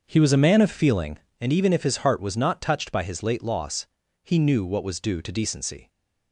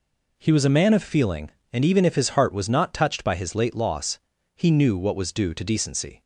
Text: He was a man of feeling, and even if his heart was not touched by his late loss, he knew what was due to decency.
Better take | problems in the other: second | starts louder than the rest; until 1.4 s; 6.5 dB

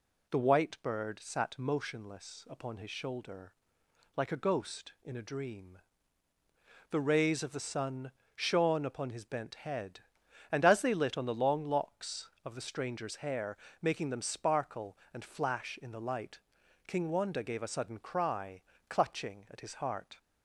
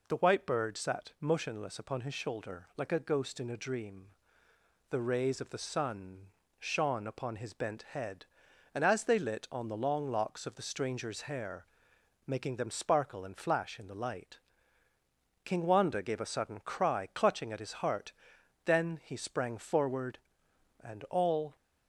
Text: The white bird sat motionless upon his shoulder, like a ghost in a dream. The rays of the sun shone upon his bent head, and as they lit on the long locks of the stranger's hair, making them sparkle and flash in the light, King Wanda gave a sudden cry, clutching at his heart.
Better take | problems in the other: first | pauses between "sun" and "shone"; slight; at 6.2 s; 0.32 s long; slight in the first // goes on to say "Then he sprang forward and all"; strong; from 18.6 s on; 2.9 s long

